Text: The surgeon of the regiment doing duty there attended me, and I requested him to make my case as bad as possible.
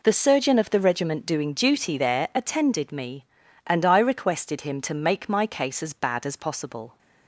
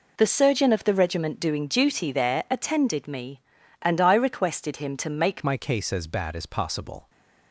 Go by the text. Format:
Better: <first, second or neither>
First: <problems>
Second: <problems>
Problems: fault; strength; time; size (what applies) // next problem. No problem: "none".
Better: first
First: none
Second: changes voice at "my"; from 5.4 s on; 1.6 s long